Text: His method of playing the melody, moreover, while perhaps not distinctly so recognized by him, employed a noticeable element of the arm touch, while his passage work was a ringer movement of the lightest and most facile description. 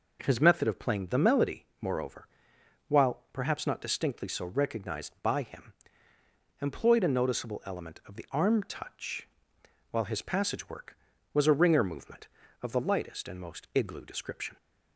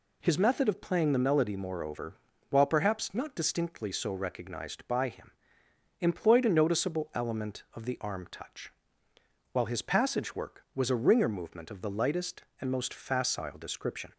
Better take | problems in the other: second | says "igloo" for "facile"; at 13.7 s

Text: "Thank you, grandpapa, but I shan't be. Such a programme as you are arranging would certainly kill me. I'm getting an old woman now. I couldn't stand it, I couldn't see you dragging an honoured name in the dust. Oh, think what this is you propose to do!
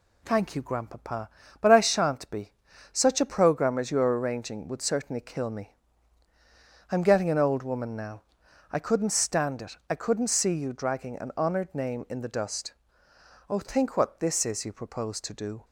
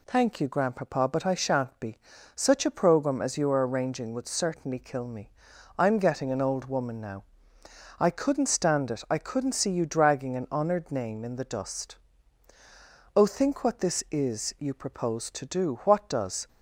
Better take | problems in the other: first | goes on to say "What does"; noticeable; from 15.8 s on; 0.64 s long

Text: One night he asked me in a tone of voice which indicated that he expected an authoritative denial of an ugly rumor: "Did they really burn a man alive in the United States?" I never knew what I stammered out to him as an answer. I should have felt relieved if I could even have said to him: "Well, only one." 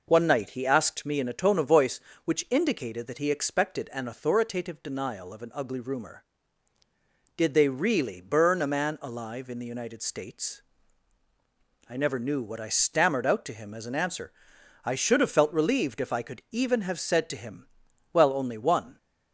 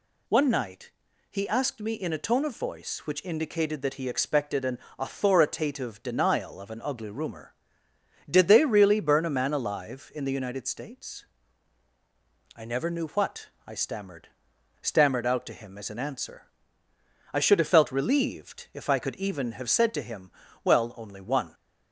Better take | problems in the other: first | pauses between "night" and "he"; at 0.8 s; 0.40 s long // pauses between "an" and "authoritative"; slight; at 4.7 s; 0.20 s long // pauses between "what" and "I"; slight; at 13.4 s; 0.18 s long // says "stammered" twice; at 14.7 s

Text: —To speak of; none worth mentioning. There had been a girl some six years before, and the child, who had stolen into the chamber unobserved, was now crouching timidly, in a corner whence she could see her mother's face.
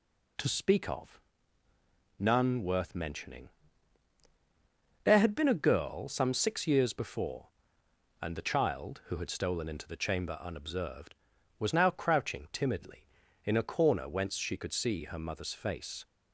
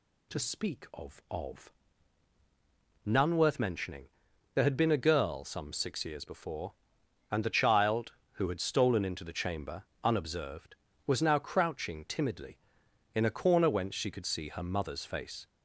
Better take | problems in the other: first | says "of" twice; at 1.3 s // pauses between "chamber" and "unobserved"; slight; at 9.8 s; 0.18 s long

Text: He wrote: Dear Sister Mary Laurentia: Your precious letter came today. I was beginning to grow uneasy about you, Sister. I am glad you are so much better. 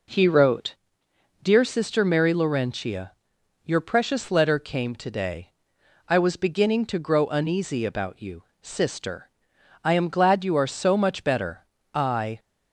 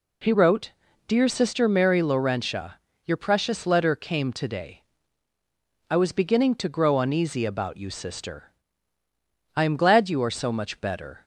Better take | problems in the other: second | goes on to say "I"; slight; from 11.9 s on; 0.46 s long

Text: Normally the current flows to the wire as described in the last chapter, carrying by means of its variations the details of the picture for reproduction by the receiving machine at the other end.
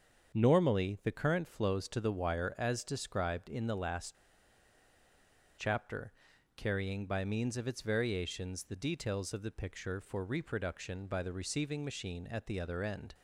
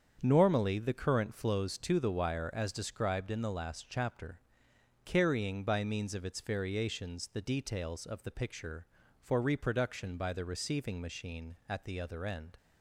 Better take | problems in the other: second | starts louder than the rest; strong; until 1.4 s; 7 dB; strong in the second // pauses between "last" and "chapter"; strong; at 4.1 s; 1.4 s long

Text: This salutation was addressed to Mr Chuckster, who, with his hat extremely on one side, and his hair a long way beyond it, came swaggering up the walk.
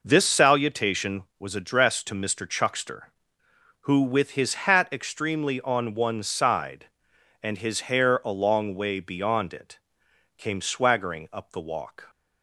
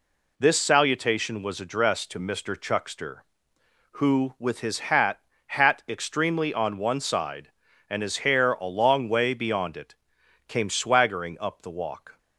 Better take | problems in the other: first | says "hat" twice; at 5.4 s

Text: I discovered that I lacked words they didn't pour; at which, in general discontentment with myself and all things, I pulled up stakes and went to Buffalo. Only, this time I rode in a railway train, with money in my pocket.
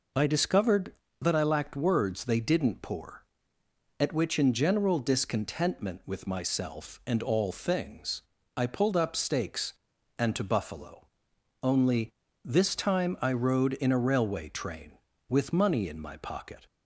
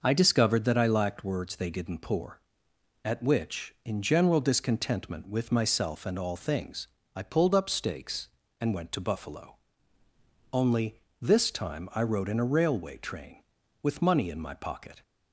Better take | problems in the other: second | skips "went"; at 10.3 s

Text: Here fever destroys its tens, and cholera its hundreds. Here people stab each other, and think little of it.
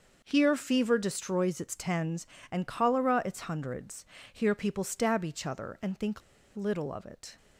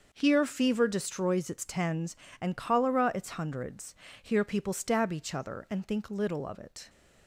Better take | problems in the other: second | starts louder than the rest; noticeable; until 1.2 s; 6 dB; noticeable in the second // pauses between "think" and "little"; slight; at 6.2 s; 0.35 s long

